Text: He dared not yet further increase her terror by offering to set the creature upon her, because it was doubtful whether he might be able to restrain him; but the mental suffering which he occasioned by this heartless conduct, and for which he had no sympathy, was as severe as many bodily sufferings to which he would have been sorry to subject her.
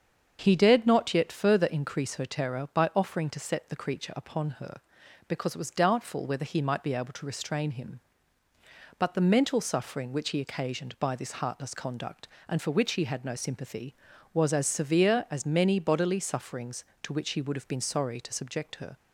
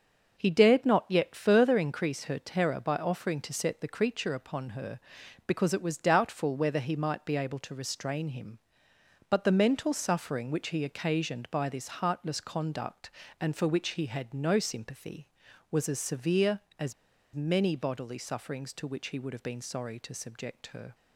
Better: first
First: starts louder than the rest; until 1.4 s; 7 dB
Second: starts louder than the rest; until 1.4 s; 6 dB // pauses between "as" and "many"; at 16.9 s; 0.41 s long

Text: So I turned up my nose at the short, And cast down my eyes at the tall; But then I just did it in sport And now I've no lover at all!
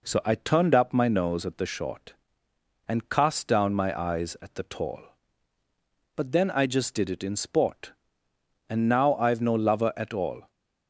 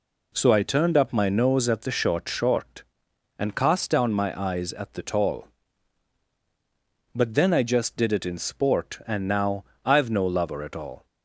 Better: first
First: none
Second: says "short" twice; at 2.2 s // pauses between "now" and "I've"; slight; at 9.6 s; 0.22 s long

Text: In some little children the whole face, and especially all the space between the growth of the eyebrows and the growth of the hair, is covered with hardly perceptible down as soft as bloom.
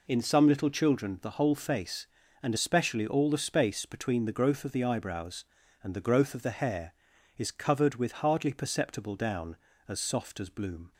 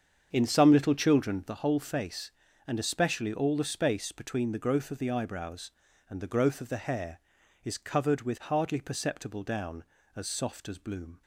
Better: first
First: none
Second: starts louder than the rest; strong; until 1.6 s; 7.5 dB

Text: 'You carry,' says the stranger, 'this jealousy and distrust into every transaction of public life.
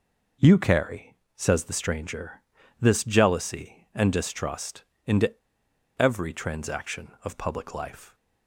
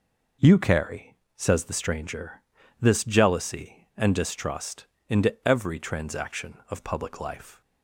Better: second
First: pauses between "distrust" and "into"; slight; at 4.8 s; 0.20 s long // pauses between "into" and "every"; noticeable; at 5.3 s; 0.68 s long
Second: pauses between "distrust" and "into"; slight; at 4.8 s; 0.20 s long

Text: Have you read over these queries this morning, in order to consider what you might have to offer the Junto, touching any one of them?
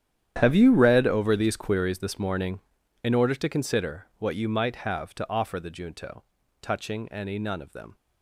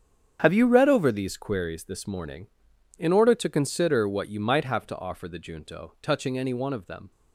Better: second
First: starts louder than the rest; strong; until 1.4 s; 10 dB // says "none" for "one"; at 7.3 s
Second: starts louder than the rest; strong; until 1.4 s; 8 dB

